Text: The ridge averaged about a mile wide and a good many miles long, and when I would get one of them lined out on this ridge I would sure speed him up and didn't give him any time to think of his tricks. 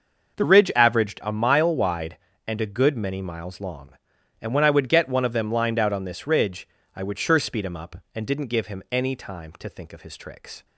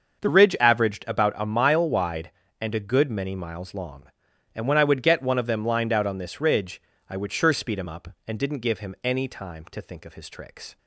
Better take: second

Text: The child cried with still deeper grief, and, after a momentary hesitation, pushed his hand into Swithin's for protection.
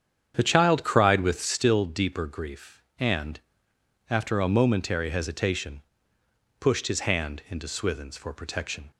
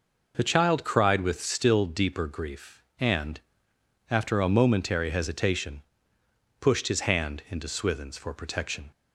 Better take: second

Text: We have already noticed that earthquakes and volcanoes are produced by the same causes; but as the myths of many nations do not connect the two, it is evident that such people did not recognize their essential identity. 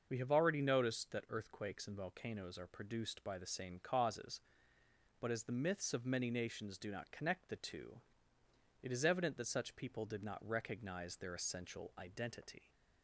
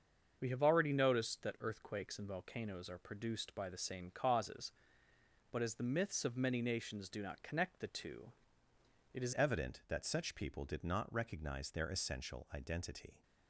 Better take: first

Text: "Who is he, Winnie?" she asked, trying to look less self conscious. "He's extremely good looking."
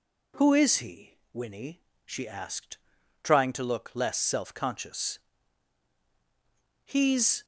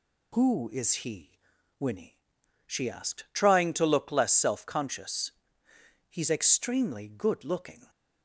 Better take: second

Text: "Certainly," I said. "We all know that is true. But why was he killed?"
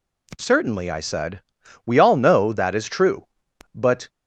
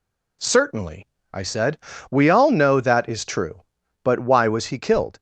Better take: second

